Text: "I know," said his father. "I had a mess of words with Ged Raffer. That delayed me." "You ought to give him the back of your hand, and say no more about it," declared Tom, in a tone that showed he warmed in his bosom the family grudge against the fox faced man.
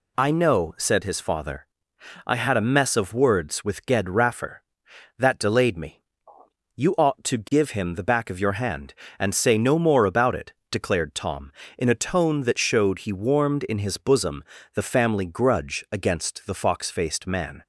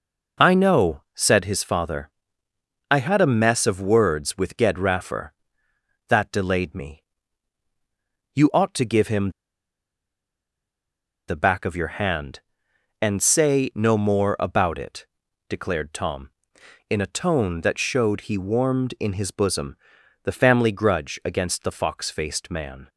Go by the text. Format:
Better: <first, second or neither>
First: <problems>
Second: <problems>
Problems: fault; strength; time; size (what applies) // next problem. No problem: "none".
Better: first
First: pauses between "bosom" and "the"; slight; at 14.4 s; 0.30 s long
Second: pauses between "him" and "the"; strong; at 9.3 s; 1.9 s long // pauses between "bosom" and "the"; noticeable; at 19.7 s; 0.48 s long